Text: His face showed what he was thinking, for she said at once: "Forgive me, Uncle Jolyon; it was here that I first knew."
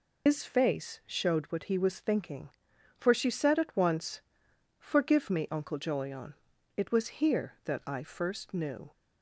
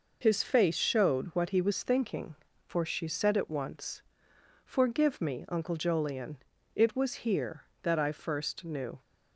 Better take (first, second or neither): second